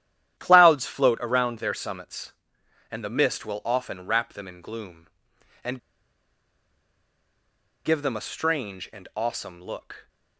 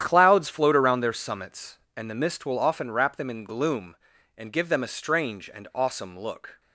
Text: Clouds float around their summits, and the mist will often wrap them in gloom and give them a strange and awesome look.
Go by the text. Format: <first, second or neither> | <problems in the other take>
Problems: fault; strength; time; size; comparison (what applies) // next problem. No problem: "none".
second | starts louder than the rest; strong; until 1.4 s; 11.5 dB; strong in the second // pauses between "and" and "give"; strong; at 5.7 s; 2.0 s long